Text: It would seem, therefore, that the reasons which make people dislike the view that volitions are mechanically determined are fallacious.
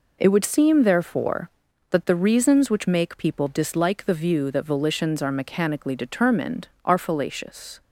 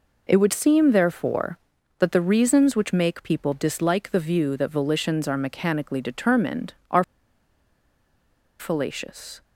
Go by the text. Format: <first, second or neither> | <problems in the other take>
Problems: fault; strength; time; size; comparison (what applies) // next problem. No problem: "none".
first | pauses between "are" and "fallacious"; strong; at 7.0 s; 1.5 s long